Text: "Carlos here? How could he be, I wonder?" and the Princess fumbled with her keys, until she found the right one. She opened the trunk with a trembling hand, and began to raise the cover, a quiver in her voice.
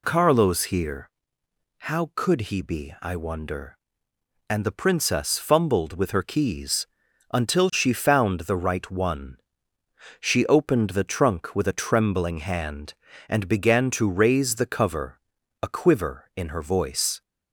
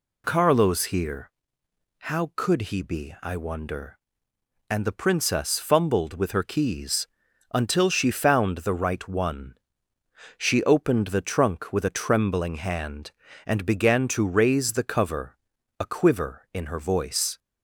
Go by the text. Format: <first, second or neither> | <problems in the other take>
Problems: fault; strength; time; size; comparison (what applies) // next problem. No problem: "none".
neither | none